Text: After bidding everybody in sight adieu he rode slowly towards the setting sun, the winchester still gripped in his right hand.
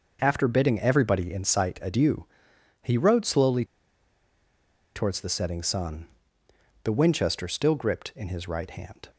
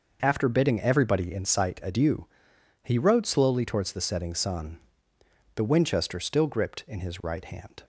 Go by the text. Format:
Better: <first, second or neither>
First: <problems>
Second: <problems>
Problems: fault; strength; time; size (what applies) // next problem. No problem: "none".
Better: second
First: pauses between "adieu" and "he"; noticeable; at 2.2 s; 0.56 s long // pauses between "slowly" and "towards"; strong; at 3.6 s; 1.3 s long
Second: pauses between "adieu" and "he"; noticeable; at 2.2 s; 0.56 s long